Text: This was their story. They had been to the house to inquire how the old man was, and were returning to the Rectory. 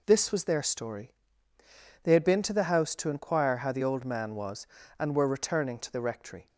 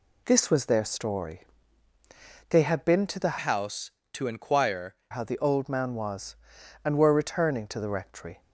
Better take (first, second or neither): first